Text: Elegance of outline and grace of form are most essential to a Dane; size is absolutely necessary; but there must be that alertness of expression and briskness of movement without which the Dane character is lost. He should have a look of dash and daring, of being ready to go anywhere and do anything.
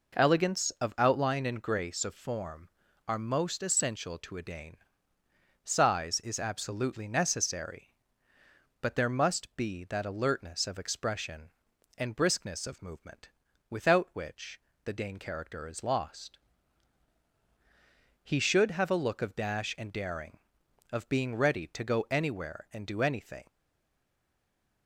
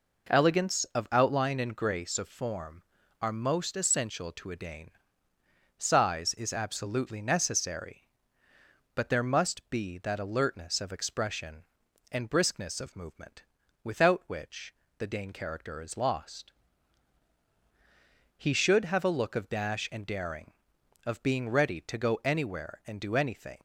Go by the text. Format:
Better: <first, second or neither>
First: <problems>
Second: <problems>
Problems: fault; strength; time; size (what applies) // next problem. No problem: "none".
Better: second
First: pauses between "movement" and "without"; at 13.2 s; 0.42 s long // pauses between "which" and "the"; slight; at 14.5 s; 0.24 s long // stays silent after the last word; noticeable; from 23.4 s on; 1.4 s long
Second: pauses between "movement" and "without"; at 13.4 s; 0.42 s long // pauses between "which" and "the"; slight; at 14.7 s; 0.24 s long